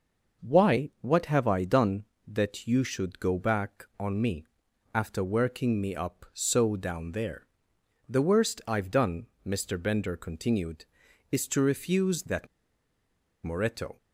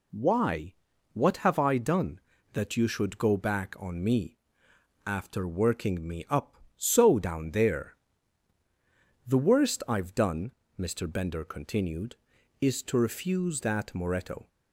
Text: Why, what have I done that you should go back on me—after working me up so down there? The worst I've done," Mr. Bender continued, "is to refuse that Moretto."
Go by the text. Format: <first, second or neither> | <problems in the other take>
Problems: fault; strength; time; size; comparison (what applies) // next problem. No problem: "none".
second | pauses between "that" and "Moretto"; noticeable; at 12.4 s; 0.96 s long